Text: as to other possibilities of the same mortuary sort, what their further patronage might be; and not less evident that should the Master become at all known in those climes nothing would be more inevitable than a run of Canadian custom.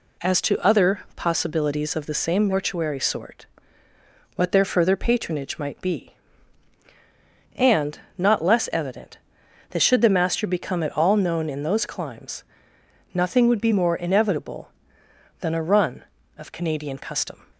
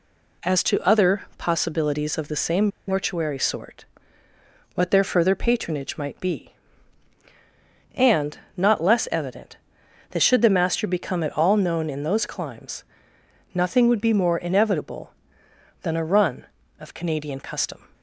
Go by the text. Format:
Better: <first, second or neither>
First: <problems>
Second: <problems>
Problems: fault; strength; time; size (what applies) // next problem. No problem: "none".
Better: first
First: pauses between "other" and "possibilities"; slight; at 1.0 s; 0.16 s long // pauses between "and" and "not"; slight; at 8.0 s; 0.16 s long // pauses between "climes" and "nothing"; noticeable; at 12.4 s; 0.70 s long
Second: pauses between "other" and "possibilities"; slight; at 1.2 s; 0.16 s long // pauses between "same" and "mortuary"; slight; at 2.6 s; 0.19 s long // pauses between "and" and "not"; slight; at 8.3 s; 0.16 s long // pauses between "climes" and "nothing"; noticeable; at 12.8 s; 0.70 s long